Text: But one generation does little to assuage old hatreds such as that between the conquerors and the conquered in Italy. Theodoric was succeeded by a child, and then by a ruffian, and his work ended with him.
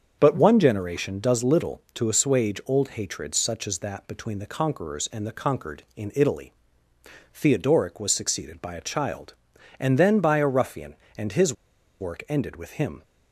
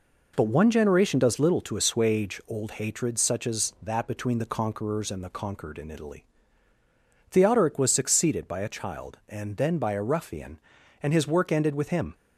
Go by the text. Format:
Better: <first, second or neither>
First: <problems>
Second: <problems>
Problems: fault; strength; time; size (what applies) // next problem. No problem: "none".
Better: second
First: starts louder than the rest; until 1.1 s; 7 dB // pauses between "his" and "work"; noticeable; at 11.5 s; 0.47 s long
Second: none